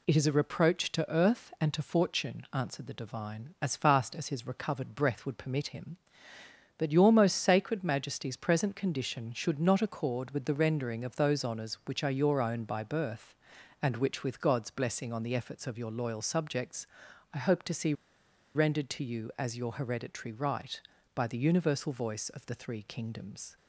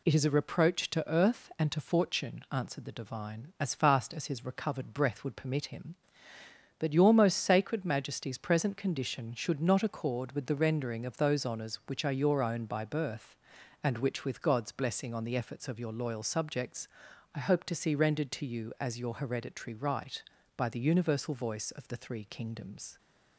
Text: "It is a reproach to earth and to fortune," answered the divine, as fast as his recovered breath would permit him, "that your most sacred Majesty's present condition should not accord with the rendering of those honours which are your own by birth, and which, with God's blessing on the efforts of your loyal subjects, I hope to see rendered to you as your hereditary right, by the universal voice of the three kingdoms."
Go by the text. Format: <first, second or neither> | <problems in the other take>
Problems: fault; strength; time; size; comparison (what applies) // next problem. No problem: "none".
second | pauses between "see" and "rendered"; noticeable; at 17.9 s; 0.62 s long